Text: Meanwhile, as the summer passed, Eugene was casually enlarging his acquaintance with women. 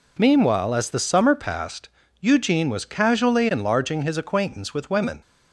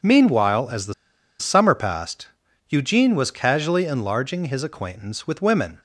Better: first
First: none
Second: pauses between "the" and "summer"; noticeable; at 0.9 s; 0.46 s long

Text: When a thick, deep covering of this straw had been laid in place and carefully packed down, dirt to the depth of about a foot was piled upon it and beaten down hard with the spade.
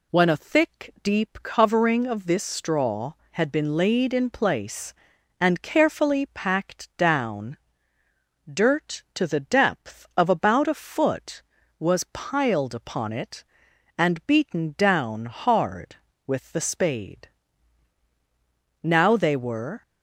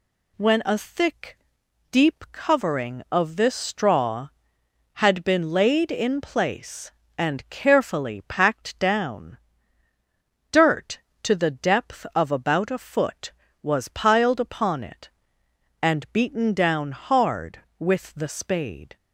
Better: second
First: goes on to say "Now they were"; noticeable; from 18.8 s on; 1.0 s long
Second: none

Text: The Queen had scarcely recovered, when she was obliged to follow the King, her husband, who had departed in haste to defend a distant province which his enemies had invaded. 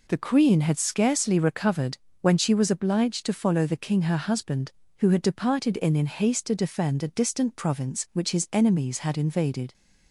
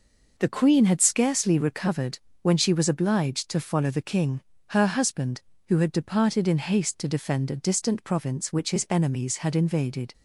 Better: second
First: says "in" twice; at 5.9 s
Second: none

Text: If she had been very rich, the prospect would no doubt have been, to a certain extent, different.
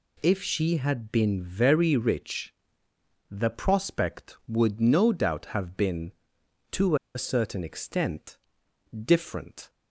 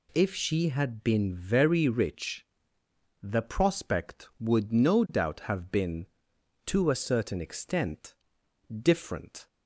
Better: second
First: pauses between "to" and "a"; slight; at 6.9 s; 0.18 s long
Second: none

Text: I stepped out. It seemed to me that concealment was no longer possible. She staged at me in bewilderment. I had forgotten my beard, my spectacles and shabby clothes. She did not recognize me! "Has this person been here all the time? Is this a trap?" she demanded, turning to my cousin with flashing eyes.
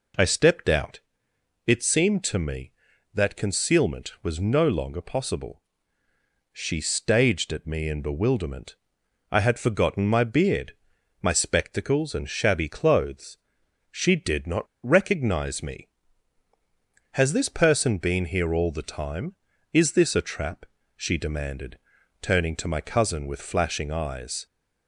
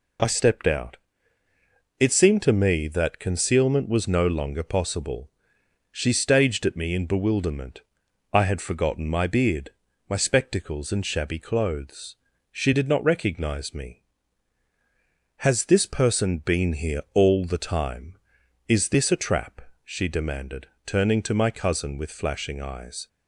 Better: second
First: pauses between "not" and "recognize"; slight; at 14.6 s; 0.18 s long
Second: none

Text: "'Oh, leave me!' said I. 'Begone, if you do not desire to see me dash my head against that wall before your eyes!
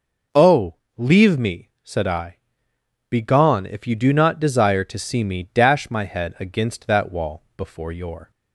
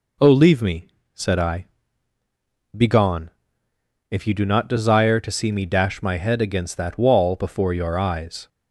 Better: second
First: stops before "eyes"; at 8.3 s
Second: none

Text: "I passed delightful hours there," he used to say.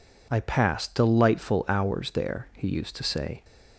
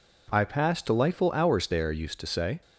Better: first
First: none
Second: skips "he"; at 1.9 s

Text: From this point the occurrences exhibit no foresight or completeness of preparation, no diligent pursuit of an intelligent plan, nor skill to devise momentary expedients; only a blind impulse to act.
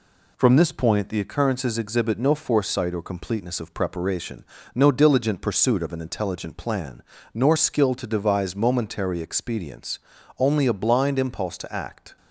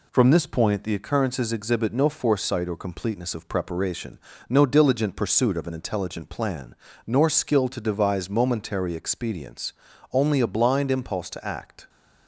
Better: neither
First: none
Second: none

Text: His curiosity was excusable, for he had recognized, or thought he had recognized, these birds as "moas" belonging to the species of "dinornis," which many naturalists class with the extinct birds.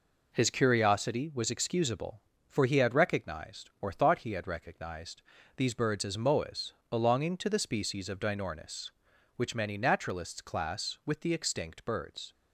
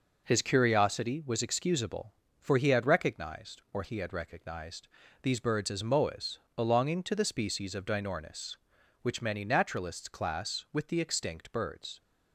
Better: first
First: pauses between "moas" and "belonging"; slight; at 6.7 s; 0.16 s long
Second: skips "thought"; at 3.8 s // pauses between "moas" and "belonging"; slight; at 6.3 s; 0.16 s long

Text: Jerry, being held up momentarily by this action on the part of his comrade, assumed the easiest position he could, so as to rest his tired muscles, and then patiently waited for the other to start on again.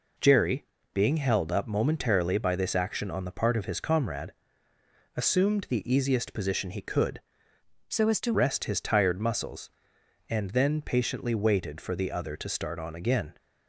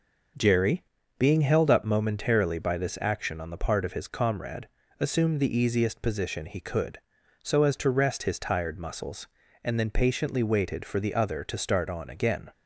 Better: second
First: changes voice from "so" to "to"; from 7.8 to 8.3 s; 0.5 s long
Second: none

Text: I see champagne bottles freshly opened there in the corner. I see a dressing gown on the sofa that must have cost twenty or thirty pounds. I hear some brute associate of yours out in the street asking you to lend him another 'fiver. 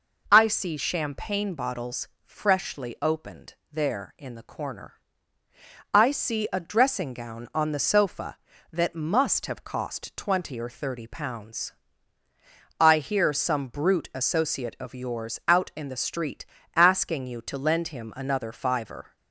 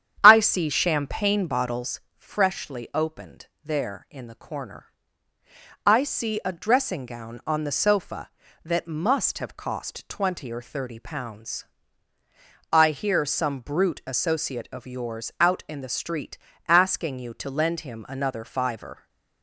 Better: first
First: pauses between "bottles" and "freshly"; slight; at 2.0 s; 0.16 s long // pauses between "opened" and "there"; slight; at 3.5 s; 0.16 s long // pauses between "street" and "asking"; slight; at 16.4 s; 0.30 s long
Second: starts louder than the rest; strong; until 1.9 s; 9 dB // pauses between "bottles" and "freshly"; slight; at 2.0 s; 0.16 s long // pauses between "opened" and "there"; slight; at 3.4 s; 0.16 s long // pauses between "street" and "asking"; slight; at 16.3 s; 0.30 s long

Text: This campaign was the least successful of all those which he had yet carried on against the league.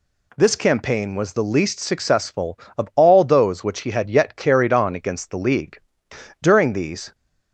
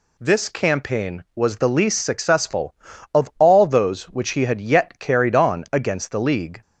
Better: second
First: goes on to say "During these"; noticeable; from 6.4 s on; 0.72 s long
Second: none

